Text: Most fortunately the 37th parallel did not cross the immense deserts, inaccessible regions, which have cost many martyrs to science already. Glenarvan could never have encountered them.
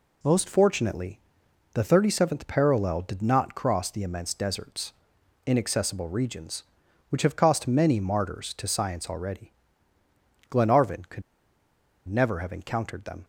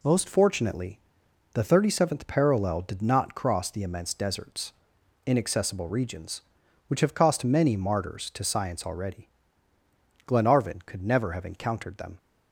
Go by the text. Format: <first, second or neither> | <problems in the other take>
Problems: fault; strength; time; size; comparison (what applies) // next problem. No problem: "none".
second | pauses between "fortunately" and "the"; noticeable; at 1.1 s; 0.54 s long; noticeable in the second // pauses between "could" and "never"; noticeable; at 11.2 s; 0.86 s long